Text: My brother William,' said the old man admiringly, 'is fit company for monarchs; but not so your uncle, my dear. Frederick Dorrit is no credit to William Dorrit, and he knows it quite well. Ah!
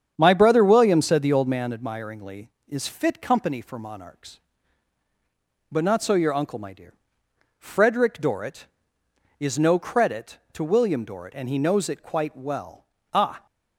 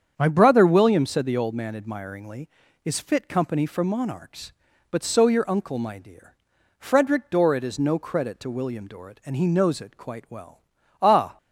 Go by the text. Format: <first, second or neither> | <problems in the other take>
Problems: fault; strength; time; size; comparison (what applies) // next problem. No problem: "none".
first | starts louder than the rest; strong; until 1.1 s; 8 dB; strong in the first // skips "not"; at 5.0 s